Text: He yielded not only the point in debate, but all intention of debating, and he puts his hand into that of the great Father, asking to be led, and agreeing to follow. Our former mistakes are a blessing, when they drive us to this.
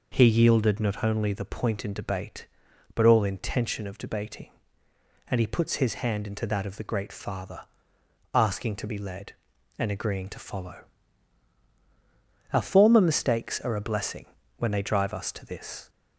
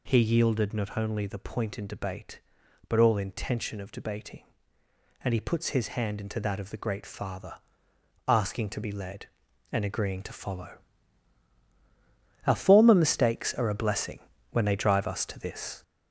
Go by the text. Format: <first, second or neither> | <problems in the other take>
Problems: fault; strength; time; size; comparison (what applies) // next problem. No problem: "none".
first | gets louder; noticeable; throughout; 4.5 dB